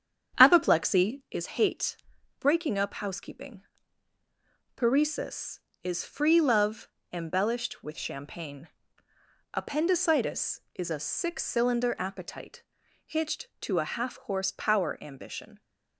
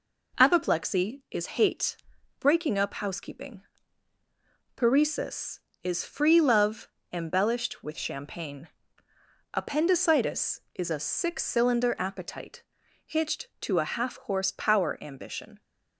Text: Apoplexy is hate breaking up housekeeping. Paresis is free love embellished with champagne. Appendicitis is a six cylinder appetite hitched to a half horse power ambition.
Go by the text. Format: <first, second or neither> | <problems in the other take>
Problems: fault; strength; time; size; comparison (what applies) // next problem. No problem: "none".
second | starts louder than the rest; strong; until 1.4 s; 8.5 dB // pauses between "hate" and "breaking"; noticeable; at 1.9 s; 0.46 s long; noticeable in the second // pauses between "love" and "embellished"; slight; at 6.8 s; 0.24 s long; slight in the second // pauses between "appetite" and "hitched"; at 12.6 s; 0.42 s long; also in the second